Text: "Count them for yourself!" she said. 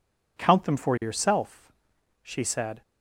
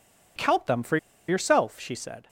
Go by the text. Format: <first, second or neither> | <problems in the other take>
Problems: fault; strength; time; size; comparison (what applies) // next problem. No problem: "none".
first | pauses between "for" and "yourself"; slight; at 0.9 s; 0.31 s long